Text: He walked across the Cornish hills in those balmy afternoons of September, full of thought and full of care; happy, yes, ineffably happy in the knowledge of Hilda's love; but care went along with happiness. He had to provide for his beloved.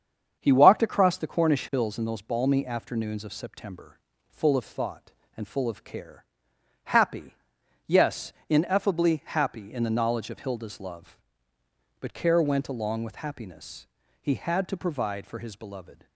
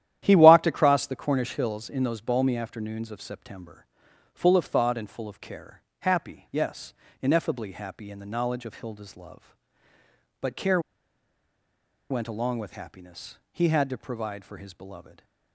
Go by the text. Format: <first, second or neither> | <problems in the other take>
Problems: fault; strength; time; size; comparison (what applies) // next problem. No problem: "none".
first | starts louder than the rest; strong; until 1.2 s; 11.5 dB; strong in the first // pauses between "care" and "went"; strong; at 10.7 s; 1.3 s long